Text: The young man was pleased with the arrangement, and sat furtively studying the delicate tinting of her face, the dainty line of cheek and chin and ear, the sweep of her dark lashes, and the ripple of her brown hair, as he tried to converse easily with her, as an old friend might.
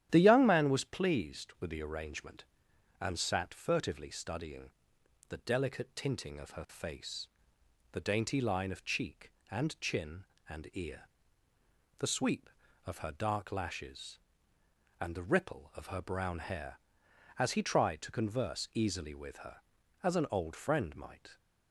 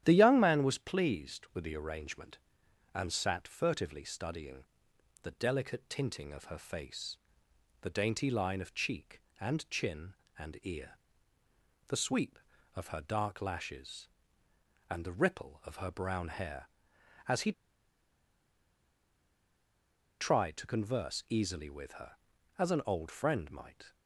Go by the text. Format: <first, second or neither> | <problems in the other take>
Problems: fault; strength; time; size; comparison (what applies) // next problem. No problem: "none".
first | starts louder than the rest; strong; until 1.0 s; 11 dB; strong in the first // pauses between "studying" and "the"; noticeable; at 4.6 s; 0.58 s long; noticeable in the first // pauses between "he" and "tried"; strong; at 17.5 s; 2.6 s long